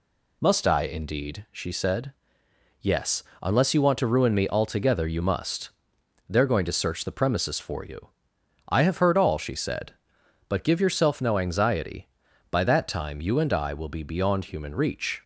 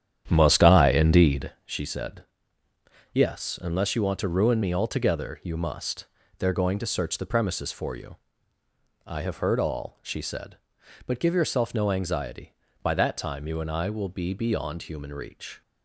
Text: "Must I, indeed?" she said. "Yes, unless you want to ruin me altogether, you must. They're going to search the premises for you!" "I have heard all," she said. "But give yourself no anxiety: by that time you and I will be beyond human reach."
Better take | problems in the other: first | starts louder than the rest; strong; until 1.6 s; 9.5 dB

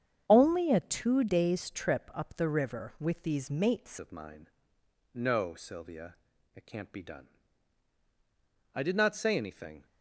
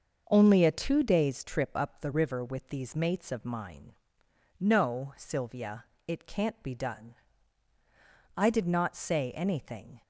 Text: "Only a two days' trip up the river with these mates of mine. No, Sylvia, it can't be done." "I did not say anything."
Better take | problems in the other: second | starts louder than the rest; strong; until 1.2 s; 8 dB; also in the second // changes voice at "of"; from 3.9 s on; 5.9 s long

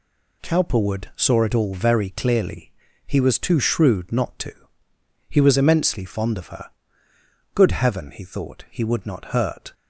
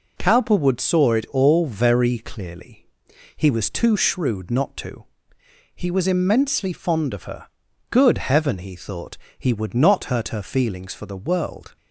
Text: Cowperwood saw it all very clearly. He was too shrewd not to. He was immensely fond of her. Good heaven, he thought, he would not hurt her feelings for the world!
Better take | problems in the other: second | stops before "her feelings for the world"; at 9.7 s

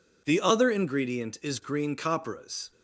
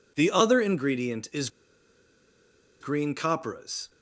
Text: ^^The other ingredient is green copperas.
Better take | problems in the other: first | pauses between "is" and "green"; strong; at 1.4 s; 1.3 s long

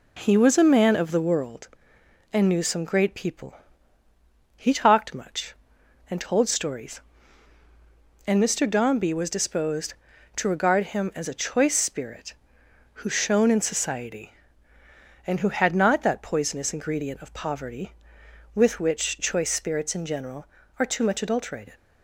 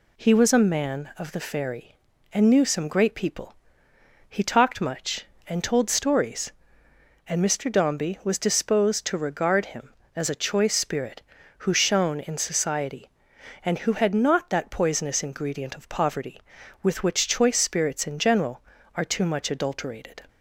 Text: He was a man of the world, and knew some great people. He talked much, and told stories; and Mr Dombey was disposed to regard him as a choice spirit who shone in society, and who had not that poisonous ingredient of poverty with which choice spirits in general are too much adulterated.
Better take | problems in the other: first | says "fairy" for "world"; at 1.4 s

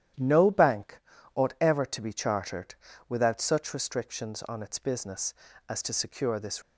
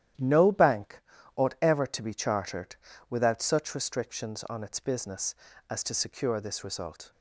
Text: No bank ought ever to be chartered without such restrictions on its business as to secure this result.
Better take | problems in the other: second | starts louder than the rest; strong; until 1.5 s; 11 dB; strong in the second // pauses between "bank" and "ought"; slight; at 0.9 s; 0.34 s long; slight in the second // pauses between "chartered" and "without"; slight; at 2.7 s; 0.32 s long; slight in the second // stops before "result"; at 6.6 s

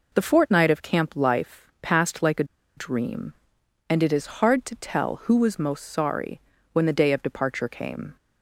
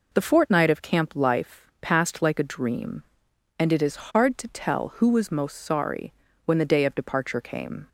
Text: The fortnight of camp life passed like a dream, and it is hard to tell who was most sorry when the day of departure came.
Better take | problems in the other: second | pauses between "a" and "dream"; slight; at 2.4 s; 0.32 s long // pauses between "sorry" and "when"; slight; at 6.3 s; 0.32 s long; slight in the second

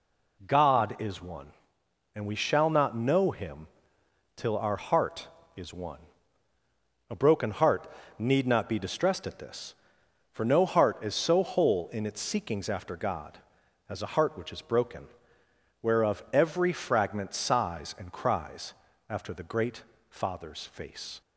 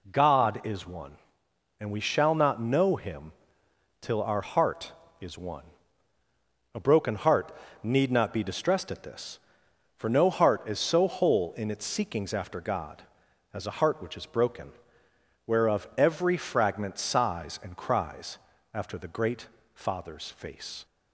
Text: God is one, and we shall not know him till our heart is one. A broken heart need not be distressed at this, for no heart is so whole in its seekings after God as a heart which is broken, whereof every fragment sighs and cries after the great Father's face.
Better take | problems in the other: neither | pauses between "him" and "till"; noticeable; the same in both // pauses between "heart" and "need"; slight; the same in both // pauses between "cries" and "after"; slight; the same in both // pauses between "great" and "Father's"; slight; the same in both

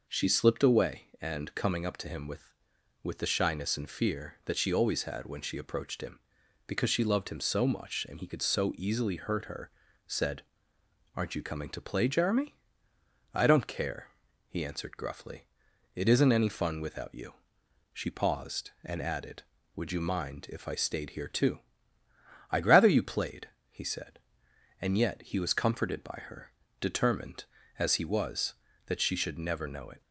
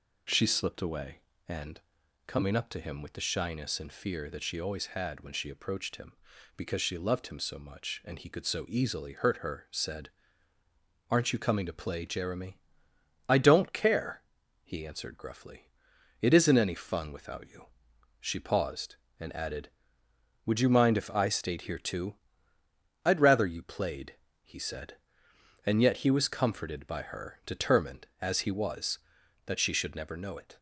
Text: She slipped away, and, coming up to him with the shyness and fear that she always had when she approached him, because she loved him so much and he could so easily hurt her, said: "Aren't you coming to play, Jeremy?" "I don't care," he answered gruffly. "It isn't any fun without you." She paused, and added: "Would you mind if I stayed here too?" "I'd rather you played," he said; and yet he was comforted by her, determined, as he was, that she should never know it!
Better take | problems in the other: second | says "with" twice; at 3.0 s

